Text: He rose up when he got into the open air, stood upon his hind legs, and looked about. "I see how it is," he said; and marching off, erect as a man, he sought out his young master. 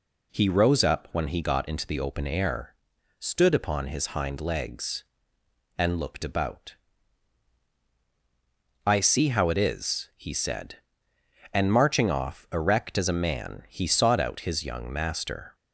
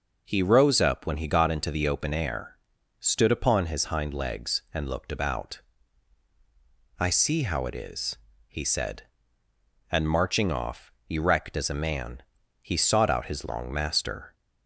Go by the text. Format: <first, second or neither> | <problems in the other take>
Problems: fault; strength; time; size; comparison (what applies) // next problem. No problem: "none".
first | says "long" for "young"; at 13.4 s